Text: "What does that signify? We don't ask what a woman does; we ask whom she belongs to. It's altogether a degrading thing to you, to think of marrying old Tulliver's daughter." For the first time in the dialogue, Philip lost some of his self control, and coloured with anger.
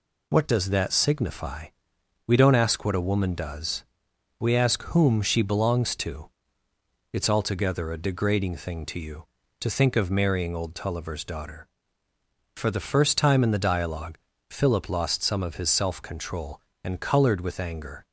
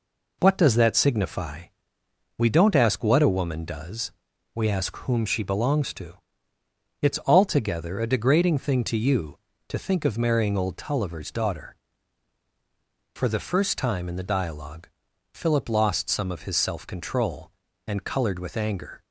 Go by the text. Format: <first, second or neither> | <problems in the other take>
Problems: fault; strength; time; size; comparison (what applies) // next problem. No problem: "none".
neither | none